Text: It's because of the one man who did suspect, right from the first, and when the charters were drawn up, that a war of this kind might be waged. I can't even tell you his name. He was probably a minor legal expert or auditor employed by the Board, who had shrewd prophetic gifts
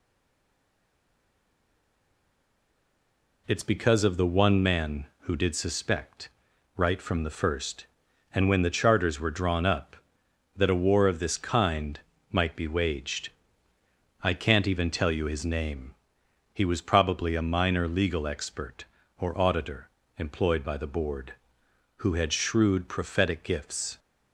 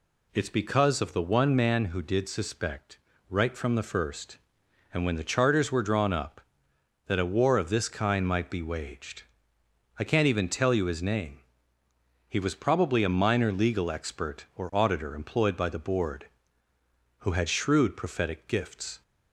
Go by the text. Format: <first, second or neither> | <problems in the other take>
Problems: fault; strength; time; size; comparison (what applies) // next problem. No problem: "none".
second | stays silent before the first word; strong; until 3.4 s; 3.4 s long // pauses between "kind" and "might"; slight; at 11.9 s; 0.32 s long // pauses between "auditor" and "employed"; slight; at 19.8 s; 0.28 s long